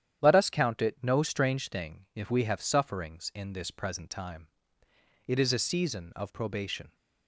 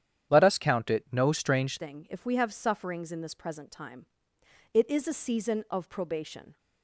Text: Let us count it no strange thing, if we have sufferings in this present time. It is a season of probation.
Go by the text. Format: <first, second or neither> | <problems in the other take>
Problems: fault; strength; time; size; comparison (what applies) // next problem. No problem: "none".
first | starts louder than the rest; strong; until 1.3 s; 9.5 dB; strong in the first // changes voice at "thing"; from 1.7 s on; 4.8 s long